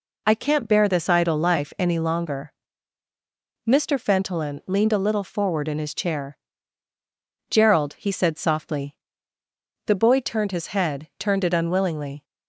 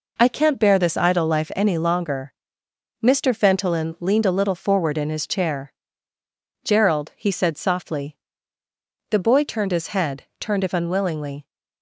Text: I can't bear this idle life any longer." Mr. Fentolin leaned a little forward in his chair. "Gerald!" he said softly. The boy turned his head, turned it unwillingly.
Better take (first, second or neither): first